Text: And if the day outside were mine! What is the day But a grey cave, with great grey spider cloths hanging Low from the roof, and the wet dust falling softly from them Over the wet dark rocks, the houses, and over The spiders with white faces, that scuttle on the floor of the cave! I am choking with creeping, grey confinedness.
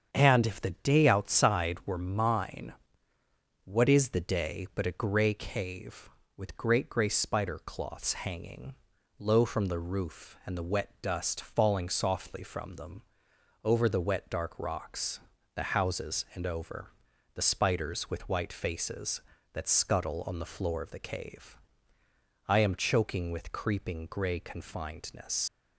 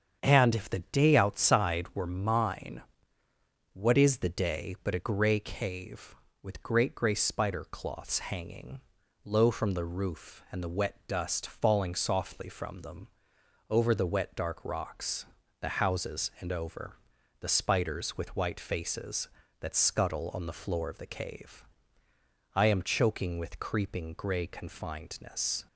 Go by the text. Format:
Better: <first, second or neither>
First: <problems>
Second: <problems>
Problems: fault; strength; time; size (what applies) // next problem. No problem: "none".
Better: second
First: starts louder than the rest; strong; until 1.1 s; 7.5 dB // pauses between "hanging" and "Low"; at 8.7 s; 0.44 s long // pauses between "them" and "Over"; noticeable; at 13.0 s; 0.60 s long // pauses between "over" and "The"; at 16.9 s; 0.44 s long // leaves "confinedness" unfinished; at 25.4 s; 120 ms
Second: starts louder than the rest; strong; until 1.2 s; 7.5 dB // pauses between "hanging" and "Low"; at 8.8 s; 0.44 s long // pauses between "them" and "Over"; noticeable; at 13.0 s; 0.60 s long // pauses between "over" and "The"; at 16.9 s; 0.44 s long